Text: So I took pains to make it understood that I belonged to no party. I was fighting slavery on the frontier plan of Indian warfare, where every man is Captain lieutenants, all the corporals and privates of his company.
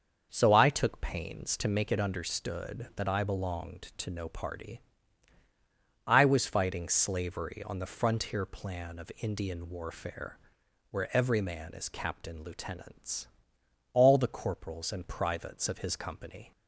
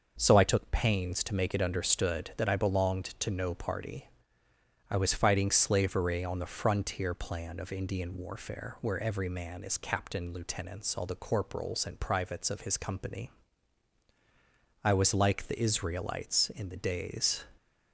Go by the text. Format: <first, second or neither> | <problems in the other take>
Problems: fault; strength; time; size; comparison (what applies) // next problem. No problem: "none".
first | starts louder than the rest; noticeable; until 1.1 s; 6 dB; also in the first // goes on to say "I was like the Israelites in the days"; strong; from 14.8 s on; 2.6 s long